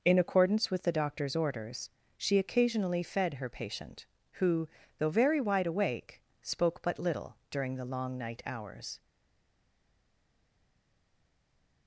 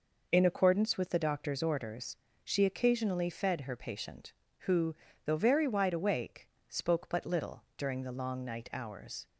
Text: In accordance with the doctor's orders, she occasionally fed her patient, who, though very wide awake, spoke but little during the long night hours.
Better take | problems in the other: second | pauses between "little" and "during"; slight; at 7.3 s; 0.16 s long; slight in the second // stays silent after the last word; strong; from 9.0 s on; 2.8 s long

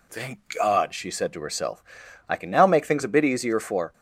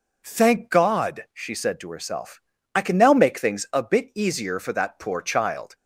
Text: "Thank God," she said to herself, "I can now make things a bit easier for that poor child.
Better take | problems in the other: second | stops before "that poor child"; at 3.9 s

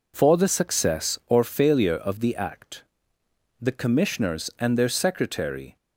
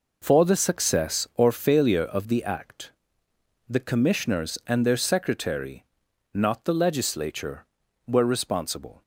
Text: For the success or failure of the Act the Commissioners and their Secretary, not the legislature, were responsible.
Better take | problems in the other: second | pauses between "Act" and "the"; noticeable; at 2.8 s; 0.76 s long; noticeable in the second // stops before "not the legislature were responsible"; at 5.7 s

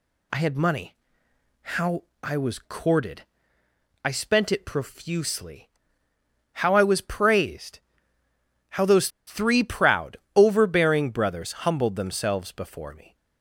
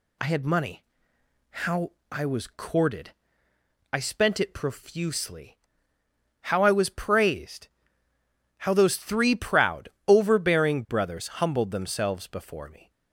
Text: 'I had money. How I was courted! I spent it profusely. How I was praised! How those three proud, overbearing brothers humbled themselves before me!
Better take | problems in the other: second | pauses between "How" and "I"; slight; at 2.0 s; 0.18 s long; slight in the second // pauses between "those" and "three"; slight; at 9.0 s; 0.18 s long

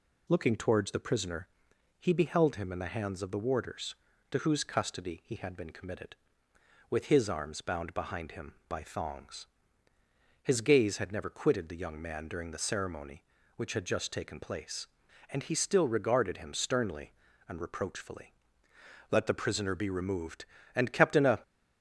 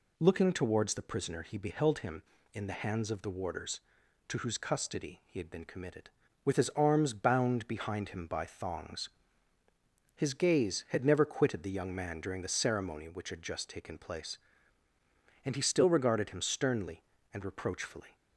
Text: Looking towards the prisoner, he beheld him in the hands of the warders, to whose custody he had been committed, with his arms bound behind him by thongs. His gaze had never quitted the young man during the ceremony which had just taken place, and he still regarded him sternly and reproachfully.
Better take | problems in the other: second | goes on to say "Let the prisoner be removed and kept in a"; strong; from 19.0 s on; 2.3 s long

